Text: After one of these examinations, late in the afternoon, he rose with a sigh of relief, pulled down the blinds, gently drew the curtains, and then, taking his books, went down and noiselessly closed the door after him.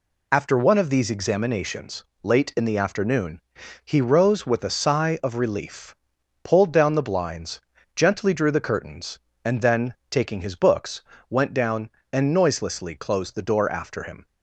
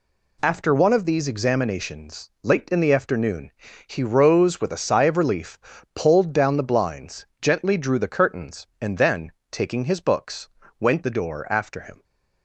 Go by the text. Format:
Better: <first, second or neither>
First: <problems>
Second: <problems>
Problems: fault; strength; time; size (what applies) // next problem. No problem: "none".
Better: first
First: none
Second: skips "down and noiselessly closed"; at 11.0 s